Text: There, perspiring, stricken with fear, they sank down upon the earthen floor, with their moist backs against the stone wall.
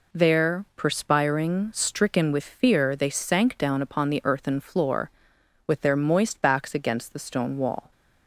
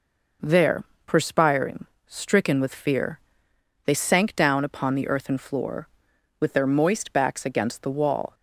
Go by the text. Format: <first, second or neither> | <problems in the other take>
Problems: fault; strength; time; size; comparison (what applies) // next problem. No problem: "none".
first | skips "stone"; at 7.8 s